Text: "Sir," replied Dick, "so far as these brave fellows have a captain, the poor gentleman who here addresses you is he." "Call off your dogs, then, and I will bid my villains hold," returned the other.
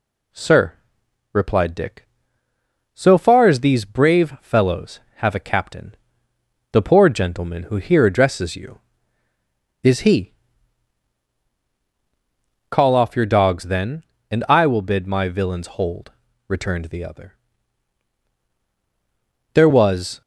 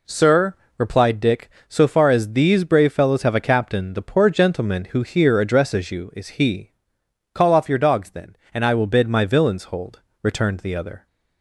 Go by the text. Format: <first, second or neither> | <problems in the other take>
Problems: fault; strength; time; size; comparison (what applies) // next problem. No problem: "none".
second | goes on to say "There was"; noticeable; from 19.5 s on; 0.67 s long